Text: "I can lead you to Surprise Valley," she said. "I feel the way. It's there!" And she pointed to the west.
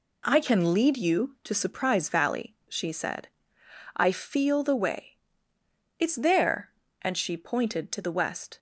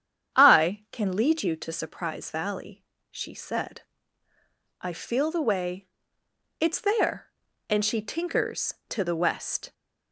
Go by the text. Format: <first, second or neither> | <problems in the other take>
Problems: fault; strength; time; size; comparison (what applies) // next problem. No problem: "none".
first | starts louder than the rest; strong; until 1.4 s; 8.5 dB // says "tinkers" for "pointed"; at 8.0 s